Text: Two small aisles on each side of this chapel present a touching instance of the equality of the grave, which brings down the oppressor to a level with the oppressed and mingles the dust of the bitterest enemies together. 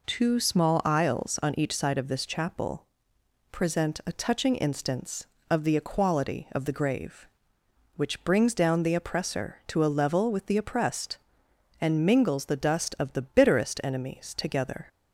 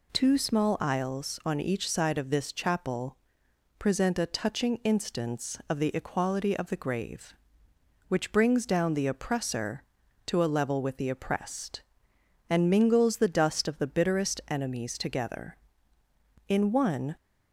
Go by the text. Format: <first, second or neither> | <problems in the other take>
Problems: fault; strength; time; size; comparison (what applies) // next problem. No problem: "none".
first | pauses between "chapel" and "present"; noticeable; at 3.1 s; 0.62 s long; noticeable in the first // goes on to say "In one"; noticeable; from 16.4 s on; 0.66 s long